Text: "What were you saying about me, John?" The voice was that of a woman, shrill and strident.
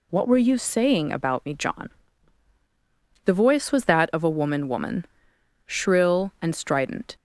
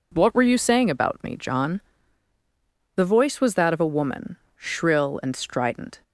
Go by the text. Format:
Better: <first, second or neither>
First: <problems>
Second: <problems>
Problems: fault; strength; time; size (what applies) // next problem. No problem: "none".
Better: second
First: says "woman" twice; at 4.6 s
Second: none